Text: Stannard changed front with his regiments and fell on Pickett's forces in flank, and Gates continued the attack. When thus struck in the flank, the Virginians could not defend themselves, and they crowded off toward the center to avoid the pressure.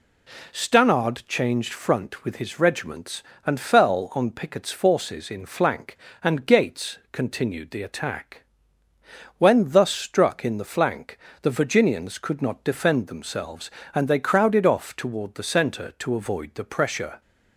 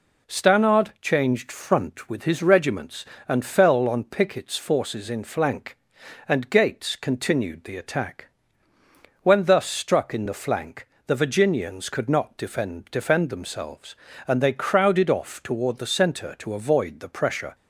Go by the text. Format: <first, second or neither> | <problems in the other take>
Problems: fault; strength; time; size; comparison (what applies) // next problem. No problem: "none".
first | says "defend" twice; at 12.9 s